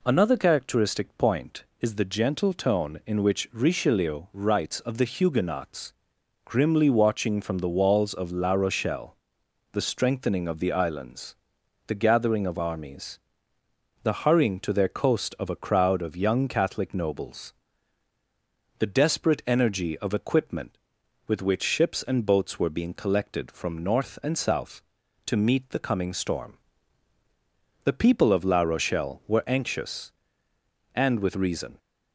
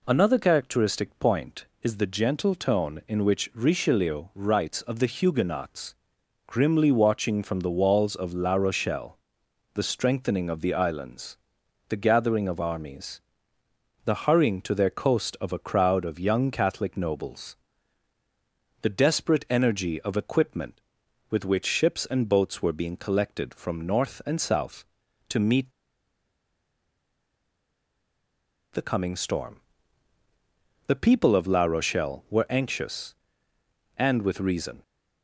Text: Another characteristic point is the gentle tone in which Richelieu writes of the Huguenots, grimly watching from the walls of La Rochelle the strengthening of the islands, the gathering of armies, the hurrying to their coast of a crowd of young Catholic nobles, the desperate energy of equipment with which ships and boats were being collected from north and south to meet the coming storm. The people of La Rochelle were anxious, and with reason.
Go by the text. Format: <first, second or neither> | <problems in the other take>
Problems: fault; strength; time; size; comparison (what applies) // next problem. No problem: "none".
first | pauses between "Rochelle" and "the"; noticeable; at 9.1 s; 0.58 s long; noticeable in the first // pauses between "meet" and "the"; strong; at 25.7 s; 3.0 s long